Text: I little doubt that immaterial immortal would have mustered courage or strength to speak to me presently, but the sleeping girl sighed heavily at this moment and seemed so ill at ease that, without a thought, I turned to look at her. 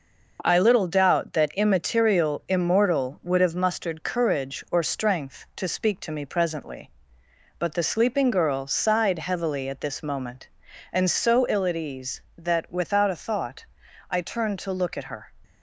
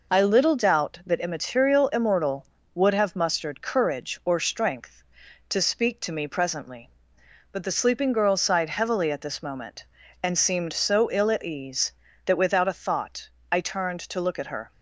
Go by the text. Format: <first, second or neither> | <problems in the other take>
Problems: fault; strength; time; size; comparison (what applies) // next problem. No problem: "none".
second | skips "seemed"; at 11.1 s